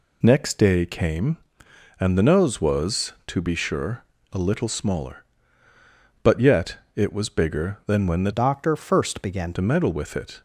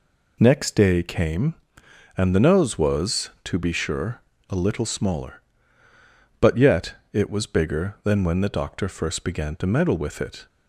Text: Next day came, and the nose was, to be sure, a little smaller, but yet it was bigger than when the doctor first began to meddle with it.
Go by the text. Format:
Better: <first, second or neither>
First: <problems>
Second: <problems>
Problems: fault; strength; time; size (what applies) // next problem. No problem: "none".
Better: second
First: pauses between "yet" and "it"; slight; at 6.7 s; 0.18 s long // changes voice from "doctor" to "began"; from 8.3 to 9.5 s; 1.2 s long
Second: pauses between "yet" and "it"; slight; at 6.9 s; 0.18 s long